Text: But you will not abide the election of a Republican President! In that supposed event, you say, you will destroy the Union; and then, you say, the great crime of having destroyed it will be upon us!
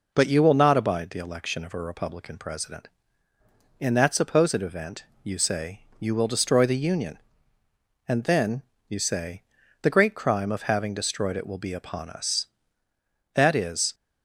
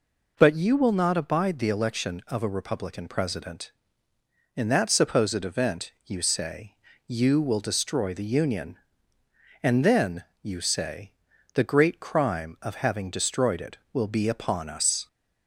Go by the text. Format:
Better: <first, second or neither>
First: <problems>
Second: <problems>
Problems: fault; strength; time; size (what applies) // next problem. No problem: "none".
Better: second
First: goes on to say "That is"; from 13.3 s on; 0.60 s long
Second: none